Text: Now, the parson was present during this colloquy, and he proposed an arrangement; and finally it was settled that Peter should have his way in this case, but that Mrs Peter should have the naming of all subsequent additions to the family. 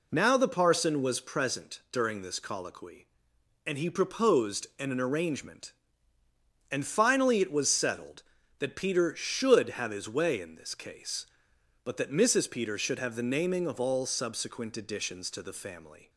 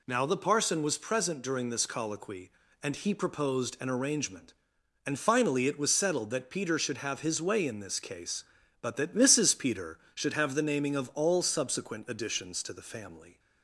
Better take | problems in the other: second | says "an" twice; at 4.8 s

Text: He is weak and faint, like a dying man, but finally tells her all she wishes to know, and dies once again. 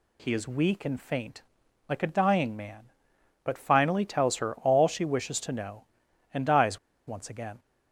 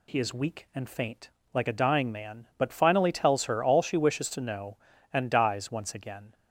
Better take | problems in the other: second | pauses between "dies" and "once"; slight; at 6.7 s; 0.28 s long

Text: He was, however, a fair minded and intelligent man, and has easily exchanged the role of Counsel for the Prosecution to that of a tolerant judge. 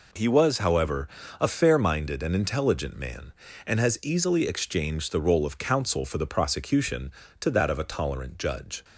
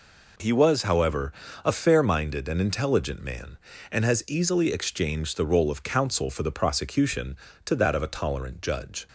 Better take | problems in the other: neither | none

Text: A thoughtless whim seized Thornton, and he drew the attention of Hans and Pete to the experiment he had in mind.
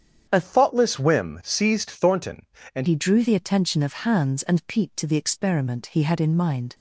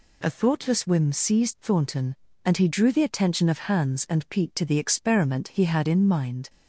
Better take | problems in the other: second | starts louder than the rest; strong; until 1.3 s; 8 dB // changes voice from "thoughtless" to "and"; from 0.4 to 2.8 s; 2.4 s long

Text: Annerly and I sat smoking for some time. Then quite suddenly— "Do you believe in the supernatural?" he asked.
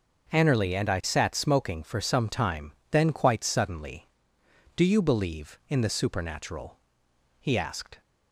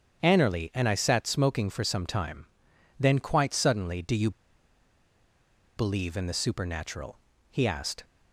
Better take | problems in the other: first | starts louder than the rest; strong; until 1.2 s; 8 dB; noticeable in the first // pauses between "you" and "believe"; strong; at 4.2 s; 1.4 s long

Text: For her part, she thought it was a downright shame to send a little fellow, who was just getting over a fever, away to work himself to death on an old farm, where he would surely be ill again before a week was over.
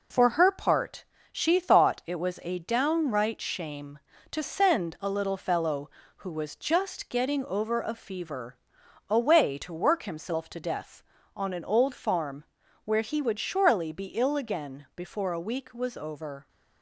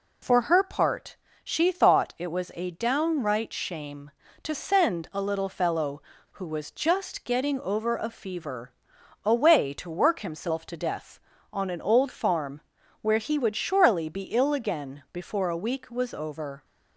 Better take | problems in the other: second | gets quieter; noticeable; throughout; 4.5 dB

